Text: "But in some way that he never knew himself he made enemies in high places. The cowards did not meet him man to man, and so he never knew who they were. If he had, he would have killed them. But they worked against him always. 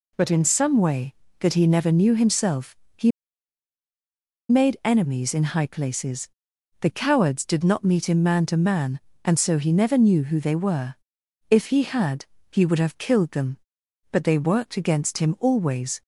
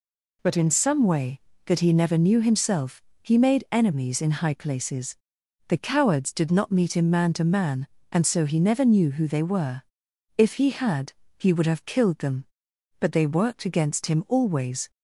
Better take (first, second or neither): second